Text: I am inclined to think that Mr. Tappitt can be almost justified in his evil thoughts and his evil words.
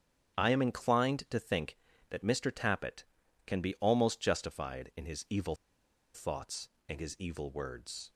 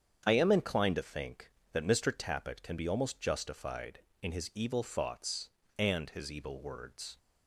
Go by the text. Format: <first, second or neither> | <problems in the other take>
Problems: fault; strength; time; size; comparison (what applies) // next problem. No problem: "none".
second | starts louder than the rest; strong; until 1.3 s; 8.5 dB; strong in the second // pauses between "evil" and "thoughts"; noticeable; at 5.5 s; 0.59 s long